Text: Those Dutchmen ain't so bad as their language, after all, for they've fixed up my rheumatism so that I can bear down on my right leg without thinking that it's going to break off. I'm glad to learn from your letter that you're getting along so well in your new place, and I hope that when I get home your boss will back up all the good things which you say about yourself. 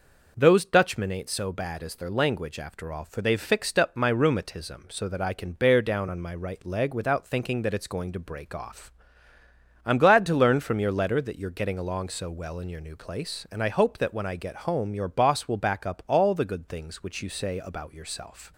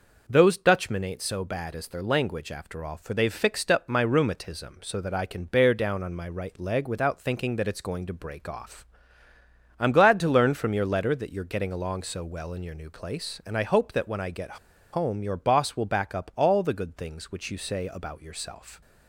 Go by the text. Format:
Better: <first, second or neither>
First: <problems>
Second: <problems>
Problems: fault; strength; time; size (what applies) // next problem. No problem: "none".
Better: first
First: none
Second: pauses between "get" and "home"; at 14.5 s; 0.36 s long